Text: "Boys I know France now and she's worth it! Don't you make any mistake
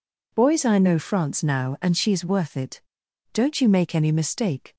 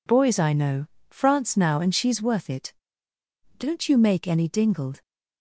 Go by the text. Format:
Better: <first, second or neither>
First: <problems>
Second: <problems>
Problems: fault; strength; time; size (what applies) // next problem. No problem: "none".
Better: first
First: none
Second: pauses between "know" and "France"; slight; at 0.8 s; 0.24 s long // says "dingled" for "mistake"; at 4.4 s